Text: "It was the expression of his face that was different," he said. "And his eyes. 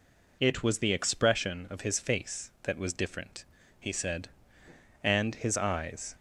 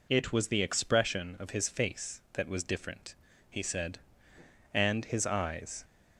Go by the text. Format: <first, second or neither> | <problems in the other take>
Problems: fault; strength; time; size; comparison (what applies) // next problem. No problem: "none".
neither | none